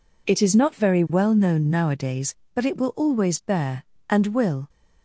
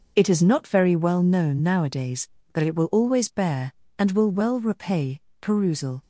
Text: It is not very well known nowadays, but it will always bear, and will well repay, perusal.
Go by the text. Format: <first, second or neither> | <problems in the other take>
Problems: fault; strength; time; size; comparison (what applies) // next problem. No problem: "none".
second | stops before "well repay perusal"; at 4.6 s